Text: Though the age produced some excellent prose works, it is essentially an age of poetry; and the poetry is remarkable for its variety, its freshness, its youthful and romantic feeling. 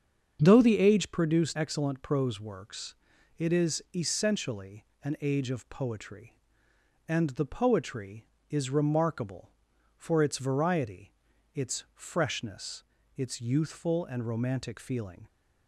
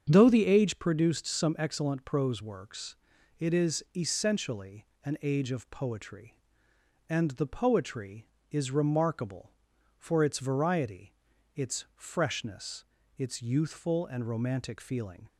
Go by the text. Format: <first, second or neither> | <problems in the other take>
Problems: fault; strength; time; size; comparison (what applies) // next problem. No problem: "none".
second | starts louder than the rest; strong; until 1.4 s; 7 dB; strong in the second // skips "some"; at 1.5 s // pauses between "essentially" and "an"; slight; at 4.8 s; 0.18 s long; slight in the second